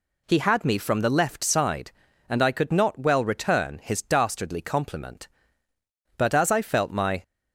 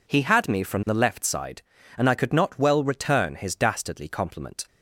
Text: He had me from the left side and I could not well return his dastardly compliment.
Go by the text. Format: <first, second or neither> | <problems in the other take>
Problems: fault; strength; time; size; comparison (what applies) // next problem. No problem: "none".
second | goes on to say "But as I felt my"; noticeable; from 6.1 s on; 1.0 s long